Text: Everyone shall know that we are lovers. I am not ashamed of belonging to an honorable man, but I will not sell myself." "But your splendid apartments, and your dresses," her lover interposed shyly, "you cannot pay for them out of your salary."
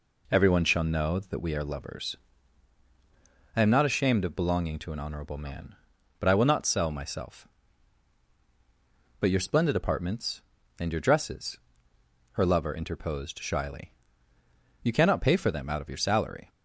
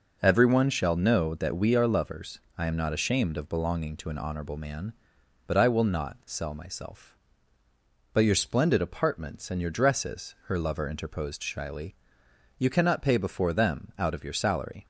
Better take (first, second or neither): first